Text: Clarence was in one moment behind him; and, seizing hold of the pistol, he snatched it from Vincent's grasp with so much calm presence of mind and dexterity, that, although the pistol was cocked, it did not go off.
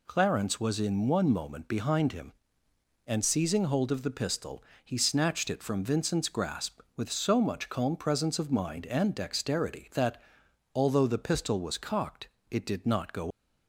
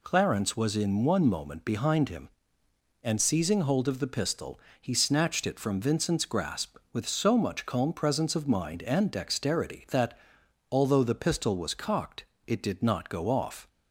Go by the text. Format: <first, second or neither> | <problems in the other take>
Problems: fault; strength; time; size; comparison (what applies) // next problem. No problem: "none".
second | stops before "off"; at 13.3 s